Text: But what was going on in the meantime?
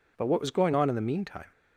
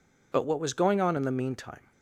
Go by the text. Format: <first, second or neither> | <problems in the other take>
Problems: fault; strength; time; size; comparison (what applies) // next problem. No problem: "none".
neither | none